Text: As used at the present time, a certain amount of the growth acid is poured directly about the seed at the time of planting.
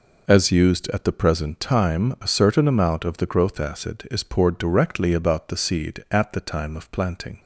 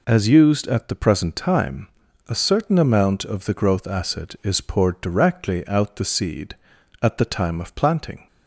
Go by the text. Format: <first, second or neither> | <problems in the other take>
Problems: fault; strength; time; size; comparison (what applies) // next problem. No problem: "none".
first | says "out" for "about"; at 5.6 s